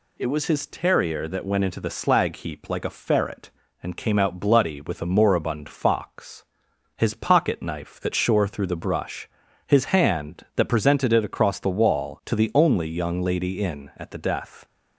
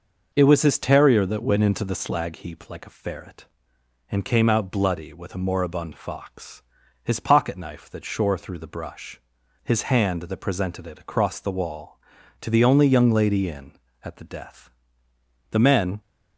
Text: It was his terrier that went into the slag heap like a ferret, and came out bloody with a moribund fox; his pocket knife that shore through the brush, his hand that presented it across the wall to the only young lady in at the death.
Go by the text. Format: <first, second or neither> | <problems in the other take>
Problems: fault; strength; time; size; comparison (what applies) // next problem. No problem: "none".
first | goes on to say "The men"; from 15.5 s on; 0.50 s long